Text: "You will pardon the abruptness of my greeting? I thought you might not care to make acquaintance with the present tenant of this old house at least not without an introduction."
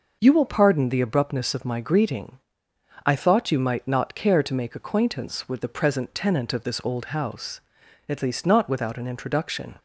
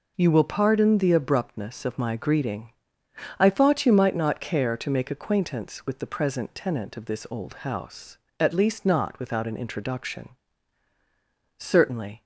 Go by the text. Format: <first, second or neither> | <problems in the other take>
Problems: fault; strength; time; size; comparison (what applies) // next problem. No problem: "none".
first | goes on to say "Certainly"; noticeable; from 11.5 s on; 0.66 s long